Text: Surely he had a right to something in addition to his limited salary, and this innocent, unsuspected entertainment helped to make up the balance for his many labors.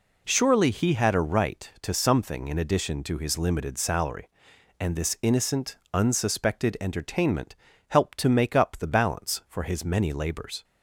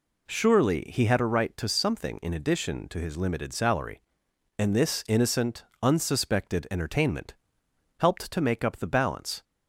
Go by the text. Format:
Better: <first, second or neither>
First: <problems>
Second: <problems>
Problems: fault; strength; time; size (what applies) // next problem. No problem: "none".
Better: first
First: pauses between "entertainment" and "helped"; slight; at 7.5 s; 0.36 s long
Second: pauses between "entertainment" and "helped"; noticeable; at 7.3 s; 0.64 s long // stops before "for his many labors"; at 9.4 s